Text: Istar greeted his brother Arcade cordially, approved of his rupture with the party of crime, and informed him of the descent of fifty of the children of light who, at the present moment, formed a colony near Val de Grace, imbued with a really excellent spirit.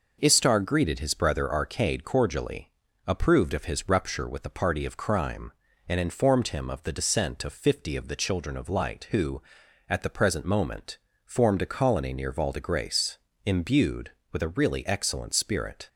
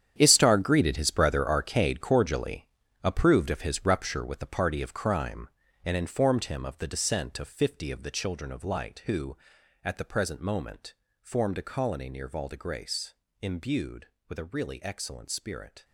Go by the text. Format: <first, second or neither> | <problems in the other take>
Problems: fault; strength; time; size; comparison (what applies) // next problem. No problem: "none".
first | gets quieter; strong; throughout; 13.5 dB